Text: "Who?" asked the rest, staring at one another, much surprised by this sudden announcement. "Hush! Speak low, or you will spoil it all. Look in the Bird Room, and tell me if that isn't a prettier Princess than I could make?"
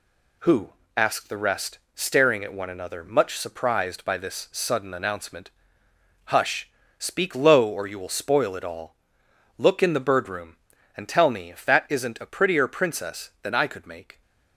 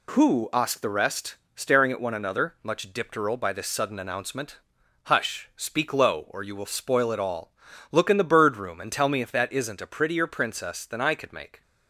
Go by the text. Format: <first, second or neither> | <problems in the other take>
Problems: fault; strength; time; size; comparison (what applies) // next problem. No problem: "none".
first | says "dipteral" for "surprised"; at 2.9 s